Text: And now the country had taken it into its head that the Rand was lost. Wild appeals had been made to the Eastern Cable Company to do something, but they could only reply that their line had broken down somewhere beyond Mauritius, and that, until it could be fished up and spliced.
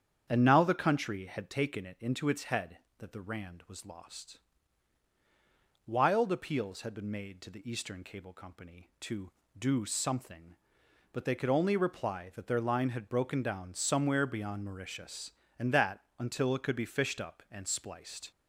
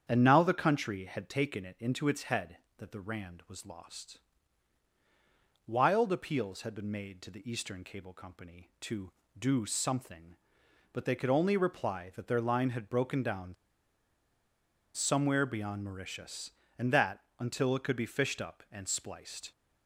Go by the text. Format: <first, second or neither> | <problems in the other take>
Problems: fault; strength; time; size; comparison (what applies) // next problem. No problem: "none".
first | starts louder than the rest; strong; until 1.0 s; 8.5 dB; strong in the first // pauses between "down" and "somewhere"; strong; at 13.5 s; 1.4 s long